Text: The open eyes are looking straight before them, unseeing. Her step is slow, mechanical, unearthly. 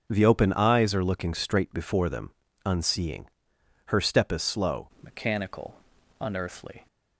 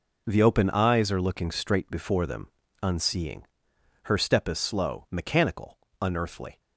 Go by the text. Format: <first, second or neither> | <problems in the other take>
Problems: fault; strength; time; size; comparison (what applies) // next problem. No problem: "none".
second | starts louder than the rest; noticeable; until 1.1 s; 6 dB // changes voice at "mechanical"; from 5.0 s on; 1.8 s long